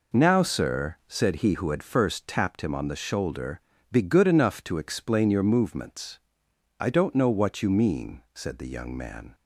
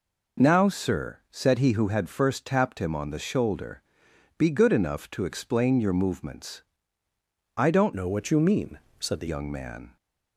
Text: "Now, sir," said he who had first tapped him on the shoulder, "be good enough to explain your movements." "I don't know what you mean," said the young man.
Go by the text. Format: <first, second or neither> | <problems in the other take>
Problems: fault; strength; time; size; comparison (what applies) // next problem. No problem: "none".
first | changes voice from "know" to "the"; from 7.9 to 9.2 s; 1.3 s long